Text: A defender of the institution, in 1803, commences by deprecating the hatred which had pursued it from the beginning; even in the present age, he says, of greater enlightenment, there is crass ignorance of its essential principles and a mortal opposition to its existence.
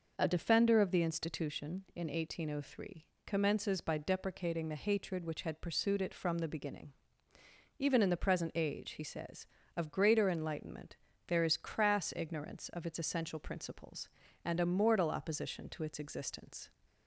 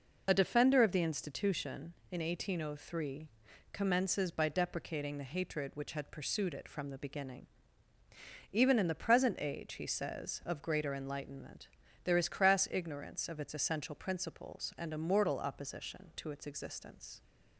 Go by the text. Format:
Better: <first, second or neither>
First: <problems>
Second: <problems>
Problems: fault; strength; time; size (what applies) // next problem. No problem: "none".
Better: neither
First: none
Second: none